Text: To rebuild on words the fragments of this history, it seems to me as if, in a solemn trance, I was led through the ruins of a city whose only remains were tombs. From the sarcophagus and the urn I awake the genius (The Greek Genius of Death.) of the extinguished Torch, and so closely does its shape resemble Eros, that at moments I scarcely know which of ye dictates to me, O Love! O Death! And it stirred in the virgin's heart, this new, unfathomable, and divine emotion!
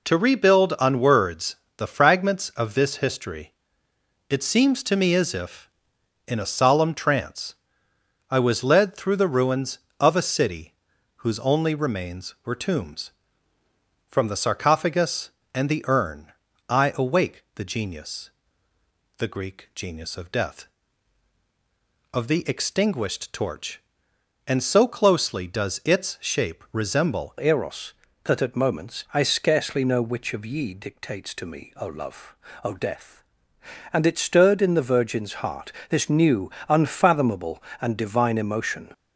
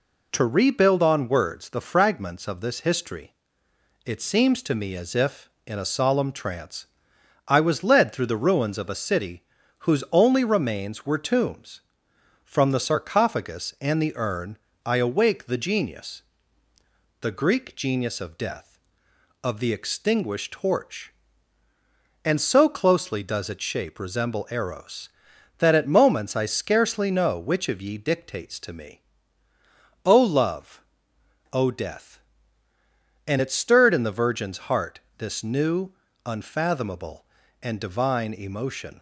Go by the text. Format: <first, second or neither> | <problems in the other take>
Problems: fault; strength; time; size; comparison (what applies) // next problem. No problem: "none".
second | pauses between "words" and "the"; slight; at 1.5 s; 0.20 s long // pauses between "city" and "whose"; at 10.7 s; 0.44 s long; slight in the second // pauses between "urn" and "I"; slight; at 16.3 s; 0.36 s long; slight in the second // changes voice at "Eros"; from 27.3 s on; 11.6 s long